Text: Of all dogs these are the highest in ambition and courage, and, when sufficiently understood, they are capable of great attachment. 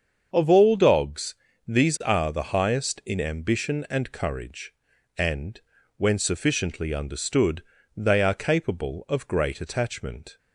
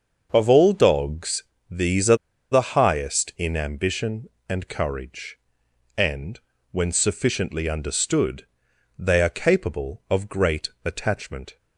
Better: first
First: starts louder than the rest; until 1.3 s; 7 dB // pauses between "dogs" and "these"; slight; at 1.3 s; 0.34 s long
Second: starts louder than the rest; until 1.3 s; 6.5 dB // pauses between "dogs" and "these"; slight; at 1.4 s; 0.26 s long // pauses between "are" and "the"; at 2.1 s; 0.37 s long

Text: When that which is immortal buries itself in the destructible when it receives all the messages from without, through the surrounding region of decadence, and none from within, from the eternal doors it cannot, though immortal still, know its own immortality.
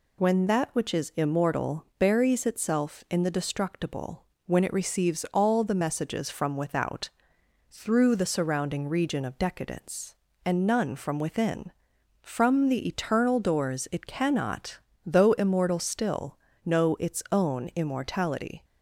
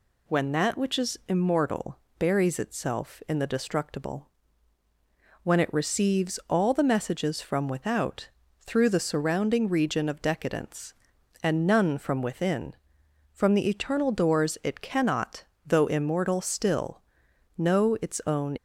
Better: first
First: pauses between "destructible" and "when"; slight; at 4.2 s; 0.22 s long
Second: pauses between "immortal" and "buries"; slight; at 1.9 s; 0.20 s long // pauses between "destructible" and "when"; at 4.2 s; 1.1 s long // stops before "immortality"; at 18.5 s

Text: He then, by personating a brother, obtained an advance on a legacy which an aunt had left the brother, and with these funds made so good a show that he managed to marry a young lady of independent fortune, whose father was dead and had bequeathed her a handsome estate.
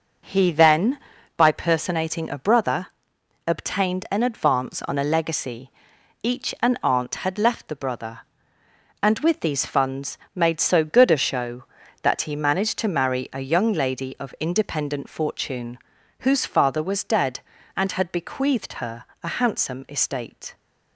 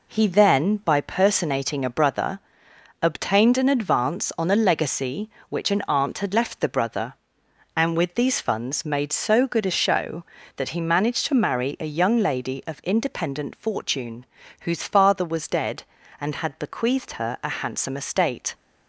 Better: second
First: says "each" for "which"; at 6.2 s // pauses between "funds" and "made"; slight; at 10.1 s; 0.18 s long // pauses between "her" and "a"; slight; at 19.0 s; 0.18 s long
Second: none

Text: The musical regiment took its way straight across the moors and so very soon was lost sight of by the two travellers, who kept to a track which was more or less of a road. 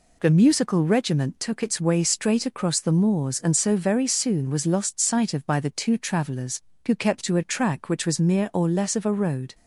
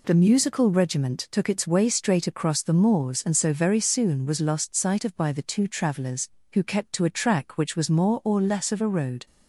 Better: second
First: says "mere" for "more"; at 8.1 s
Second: none

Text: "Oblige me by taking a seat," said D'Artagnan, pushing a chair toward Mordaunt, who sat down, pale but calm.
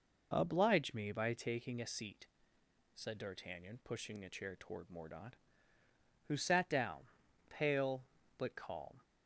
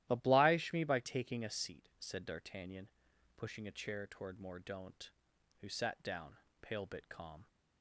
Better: first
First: none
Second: starts louder than the rest; strong; until 1.1 s; 13.5 dB // says "bit" for "but"; at 6.8 s

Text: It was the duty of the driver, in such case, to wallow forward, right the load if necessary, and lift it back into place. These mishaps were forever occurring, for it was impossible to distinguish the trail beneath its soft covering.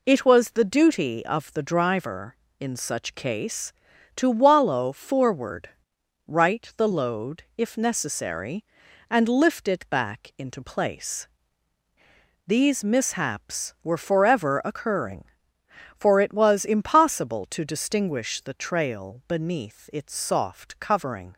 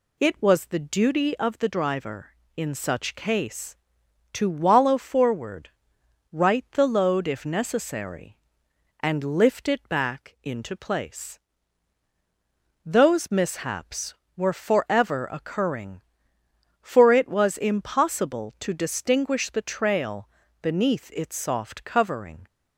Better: first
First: none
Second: says "Those" for "These"; at 12.8 s // pauses between "trail" and "beneath"; slight; at 20.2 s; 0.32 s long

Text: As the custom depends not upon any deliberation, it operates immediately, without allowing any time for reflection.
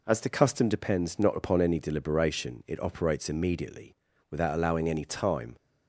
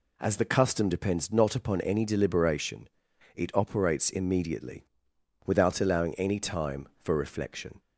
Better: second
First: stops before "for reflection"; at 5.5 s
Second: none

